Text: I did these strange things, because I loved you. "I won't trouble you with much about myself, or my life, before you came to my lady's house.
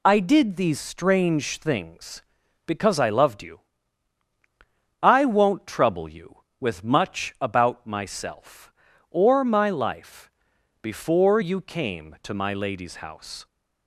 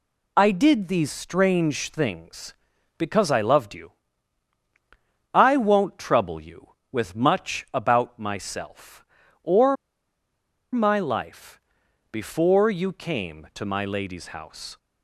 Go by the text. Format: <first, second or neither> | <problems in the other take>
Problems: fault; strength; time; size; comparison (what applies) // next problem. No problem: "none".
first | pauses between "or" and "my"; noticeable; at 9.7 s; 0.97 s long